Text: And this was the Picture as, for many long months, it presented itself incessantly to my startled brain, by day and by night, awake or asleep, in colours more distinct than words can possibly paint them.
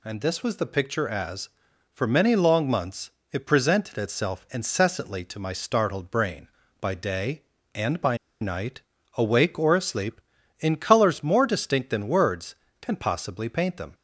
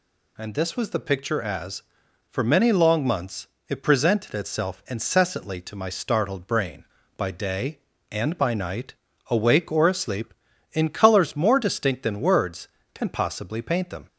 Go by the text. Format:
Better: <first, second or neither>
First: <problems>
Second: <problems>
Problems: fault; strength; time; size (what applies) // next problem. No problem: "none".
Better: second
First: pauses between "by" and "night"; slight; at 8.1 s; 0.24 s long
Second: none